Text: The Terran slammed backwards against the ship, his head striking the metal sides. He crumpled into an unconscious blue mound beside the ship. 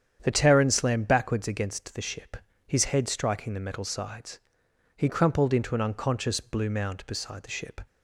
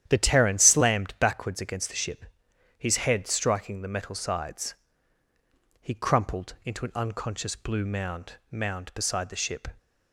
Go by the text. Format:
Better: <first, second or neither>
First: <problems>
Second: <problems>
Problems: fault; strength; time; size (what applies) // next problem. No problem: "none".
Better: first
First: starts louder than the rest; strong; until 1.2 s; 8.5 dB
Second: starts louder than the rest; strong; until 1.0 s; 10.5 dB // says "mound" twice; at 8.5 s